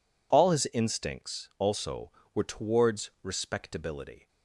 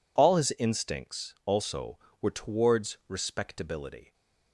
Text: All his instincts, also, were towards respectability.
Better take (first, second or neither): neither